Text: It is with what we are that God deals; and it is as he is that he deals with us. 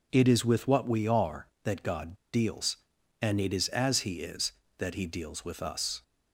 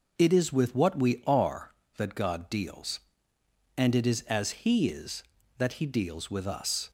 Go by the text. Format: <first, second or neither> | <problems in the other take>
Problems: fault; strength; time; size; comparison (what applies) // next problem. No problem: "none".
second | pauses between "God" and "deals"; slight; at 2.1 s; 0.17 s long